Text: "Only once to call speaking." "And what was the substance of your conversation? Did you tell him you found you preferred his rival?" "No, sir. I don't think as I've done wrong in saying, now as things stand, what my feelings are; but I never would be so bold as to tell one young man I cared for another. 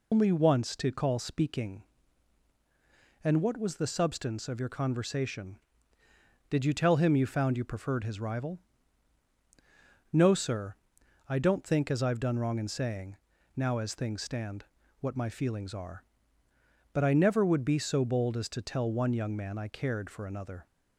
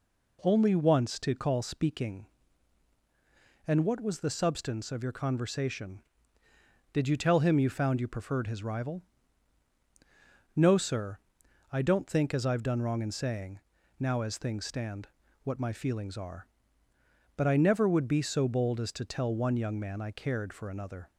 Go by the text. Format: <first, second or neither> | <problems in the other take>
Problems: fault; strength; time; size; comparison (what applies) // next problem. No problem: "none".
second | loses the start of "Only"; at 0.1 s; 160 ms